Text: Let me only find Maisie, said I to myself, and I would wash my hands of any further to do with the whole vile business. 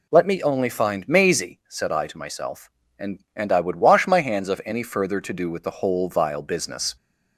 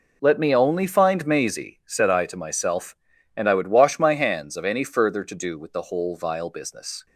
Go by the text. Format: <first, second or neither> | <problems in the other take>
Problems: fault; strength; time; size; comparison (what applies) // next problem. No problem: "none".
second | says "and" twice; at 3.3 s